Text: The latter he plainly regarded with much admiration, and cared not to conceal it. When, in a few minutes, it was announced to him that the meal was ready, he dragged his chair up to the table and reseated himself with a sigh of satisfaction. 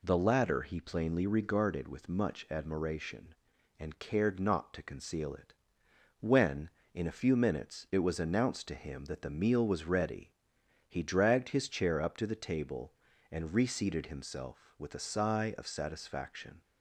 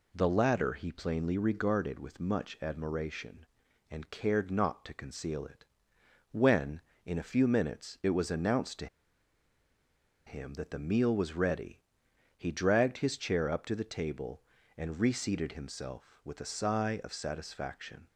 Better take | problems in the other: first | pauses between "to" and "him"; strong; at 8.8 s; 1.3 s long

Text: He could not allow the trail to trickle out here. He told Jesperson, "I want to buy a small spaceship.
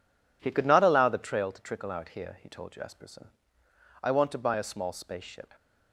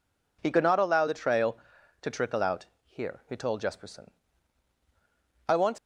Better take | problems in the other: first | pauses between "out" and "here"; slight; at 2.6 s; 0.20 s long // stops before "to buy a small spaceship"; at 5.7 s

